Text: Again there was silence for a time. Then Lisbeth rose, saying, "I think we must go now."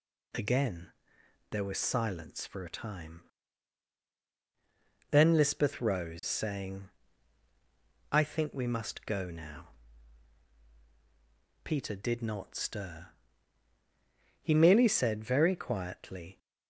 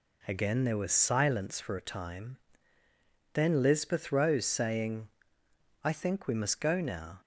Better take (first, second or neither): second